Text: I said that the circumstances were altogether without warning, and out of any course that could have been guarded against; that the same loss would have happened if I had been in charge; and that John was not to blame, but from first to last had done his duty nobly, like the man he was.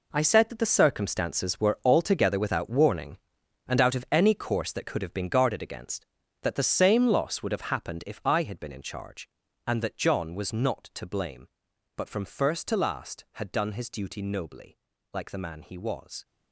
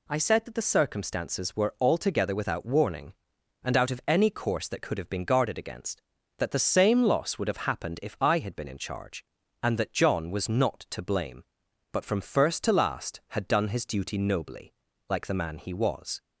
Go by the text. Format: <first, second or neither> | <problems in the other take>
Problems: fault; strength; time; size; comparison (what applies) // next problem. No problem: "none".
second | gets quieter; strong; throughout; 12.5 dB